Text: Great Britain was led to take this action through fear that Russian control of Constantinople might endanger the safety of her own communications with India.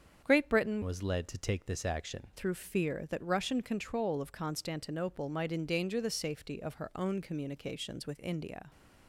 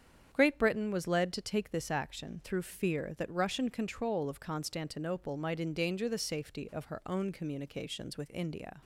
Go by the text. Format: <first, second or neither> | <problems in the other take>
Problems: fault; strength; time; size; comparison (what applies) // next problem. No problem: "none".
second | starts louder than the rest; strong; until 1.2 s; 7.5 dB; strong in the second // changes voice from "was" to "action"; from 0.8 to 2.2 s; 1.4 s long